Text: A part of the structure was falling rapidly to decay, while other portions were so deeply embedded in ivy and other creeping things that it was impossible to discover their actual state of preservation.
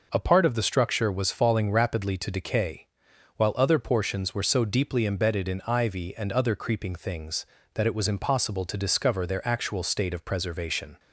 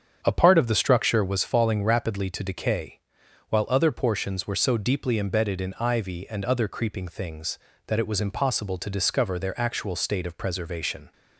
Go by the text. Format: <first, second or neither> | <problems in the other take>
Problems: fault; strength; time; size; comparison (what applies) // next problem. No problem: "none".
first | starts louder than the rest; strong; until 1.5 s; 7.5 dB